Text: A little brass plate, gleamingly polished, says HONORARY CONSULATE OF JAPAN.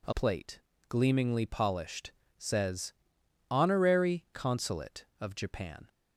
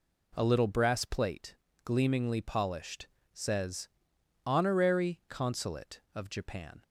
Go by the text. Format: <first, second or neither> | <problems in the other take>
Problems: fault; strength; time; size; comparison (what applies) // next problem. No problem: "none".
second | skips "little brass"; at 0.1 s // pauses between "says" and "HONORARY"; noticeable; at 2.9 s; 0.60 s long; noticeable in the second